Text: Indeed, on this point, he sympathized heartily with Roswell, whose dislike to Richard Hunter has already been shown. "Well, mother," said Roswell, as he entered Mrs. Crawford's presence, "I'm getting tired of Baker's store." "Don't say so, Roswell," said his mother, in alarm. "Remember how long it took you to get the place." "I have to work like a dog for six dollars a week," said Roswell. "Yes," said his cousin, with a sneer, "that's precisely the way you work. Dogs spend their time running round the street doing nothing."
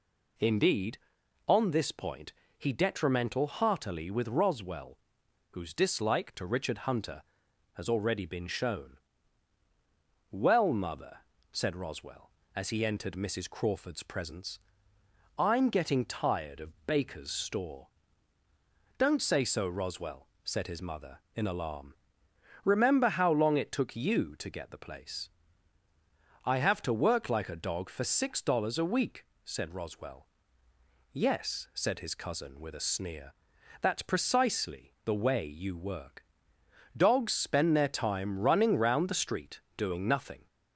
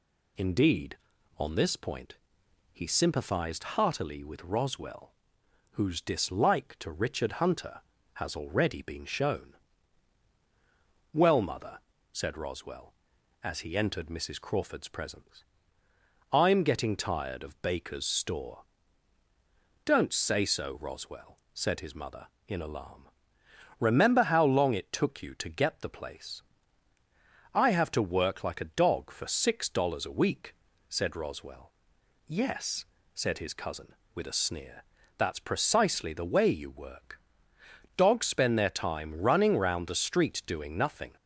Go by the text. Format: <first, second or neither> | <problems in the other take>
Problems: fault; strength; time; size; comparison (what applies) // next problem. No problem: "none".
second | says "detrimental" for "sympathized"; at 2.7 s // pauses between "street" and "doing"; slight; at 39.6 s; 0.16 s long